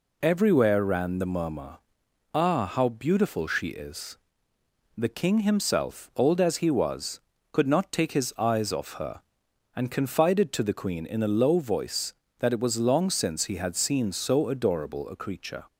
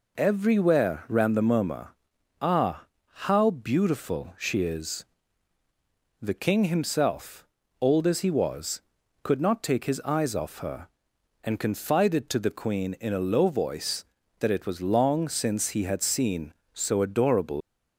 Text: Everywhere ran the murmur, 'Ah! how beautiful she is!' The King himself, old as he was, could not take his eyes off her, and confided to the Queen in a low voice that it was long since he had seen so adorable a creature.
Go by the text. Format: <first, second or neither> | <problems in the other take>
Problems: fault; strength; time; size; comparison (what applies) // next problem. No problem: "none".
first | stops before "a creature"; at 17.6 s